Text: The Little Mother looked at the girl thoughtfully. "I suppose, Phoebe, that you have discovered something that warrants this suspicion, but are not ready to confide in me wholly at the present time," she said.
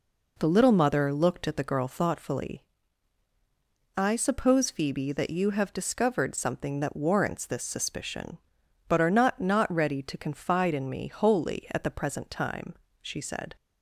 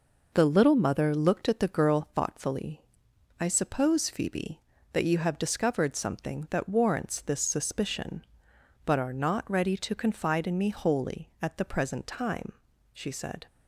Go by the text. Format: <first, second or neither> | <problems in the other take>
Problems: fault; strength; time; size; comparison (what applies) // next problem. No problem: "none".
second | says "not" twice; at 9.4 s